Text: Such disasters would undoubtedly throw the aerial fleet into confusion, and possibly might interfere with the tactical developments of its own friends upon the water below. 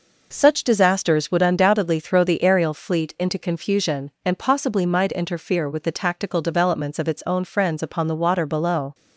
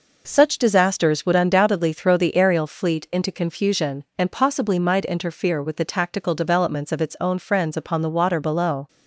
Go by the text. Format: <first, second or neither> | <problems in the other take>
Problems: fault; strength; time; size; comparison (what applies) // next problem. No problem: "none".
neither | none